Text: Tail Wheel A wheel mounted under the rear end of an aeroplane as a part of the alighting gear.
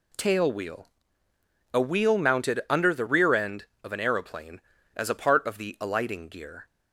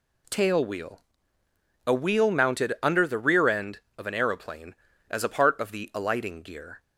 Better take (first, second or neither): neither